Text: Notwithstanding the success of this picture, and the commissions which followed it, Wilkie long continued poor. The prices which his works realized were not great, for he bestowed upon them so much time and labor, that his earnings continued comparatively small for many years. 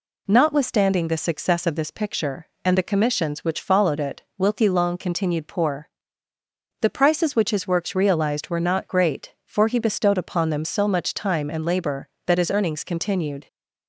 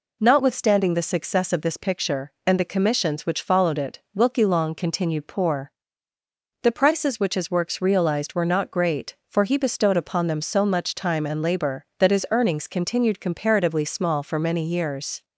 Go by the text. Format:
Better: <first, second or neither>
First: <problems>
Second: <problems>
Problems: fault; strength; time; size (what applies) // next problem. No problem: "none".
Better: second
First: stops before "comparatively small for many years"; at 13.4 s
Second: none